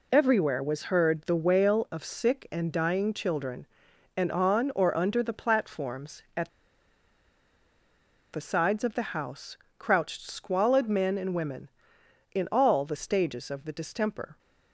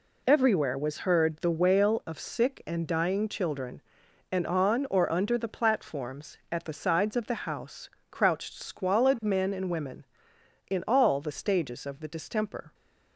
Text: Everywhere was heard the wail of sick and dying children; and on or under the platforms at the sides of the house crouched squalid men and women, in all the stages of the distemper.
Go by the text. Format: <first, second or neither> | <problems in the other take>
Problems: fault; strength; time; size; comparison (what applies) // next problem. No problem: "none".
second | pauses between "at" and "the"; strong; at 6.4 s; 1.8 s long // pauses between "house" and "crouched"; slight; at 9.5 s; 0.20 s long; slight in the second